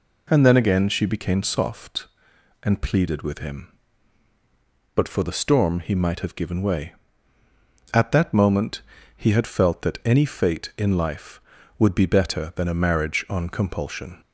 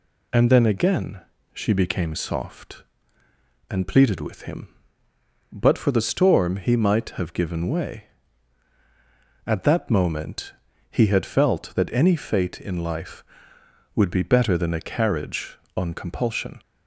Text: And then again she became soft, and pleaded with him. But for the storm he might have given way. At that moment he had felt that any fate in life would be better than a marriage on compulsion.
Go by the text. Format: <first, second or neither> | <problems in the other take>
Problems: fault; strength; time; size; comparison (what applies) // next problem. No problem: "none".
first | pauses between "again" and "she"; slight; at 1.2 s; 0.32 s long // pauses between "moment" and "he"; at 10.5 s; 0.38 s long; slight in the first // says "carriage" for "marriage"; at 14.8 s